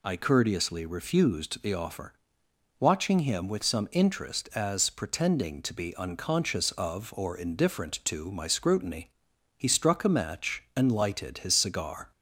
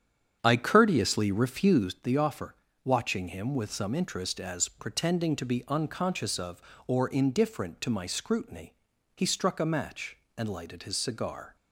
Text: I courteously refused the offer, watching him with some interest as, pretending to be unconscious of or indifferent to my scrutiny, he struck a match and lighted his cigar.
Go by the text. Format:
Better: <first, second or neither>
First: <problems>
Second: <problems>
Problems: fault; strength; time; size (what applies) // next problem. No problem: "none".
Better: first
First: none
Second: starts louder than the rest; strong; until 2.1 s; 8.5 dB